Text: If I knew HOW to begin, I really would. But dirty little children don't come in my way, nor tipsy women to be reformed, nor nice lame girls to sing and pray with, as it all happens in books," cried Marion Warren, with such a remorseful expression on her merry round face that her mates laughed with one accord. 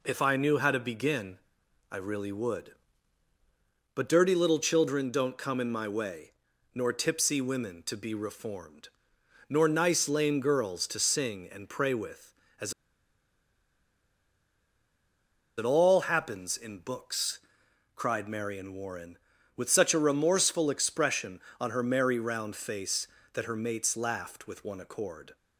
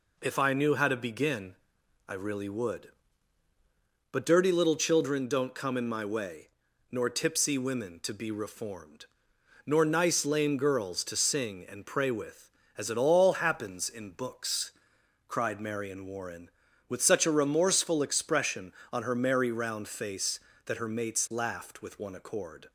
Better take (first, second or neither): second